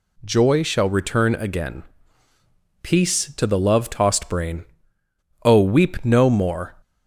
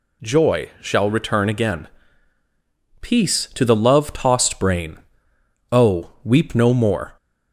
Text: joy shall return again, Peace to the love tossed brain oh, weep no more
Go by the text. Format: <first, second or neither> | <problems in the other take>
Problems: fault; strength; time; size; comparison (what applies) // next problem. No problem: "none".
neither | pauses between "brain" and "oh"; noticeable; the same in both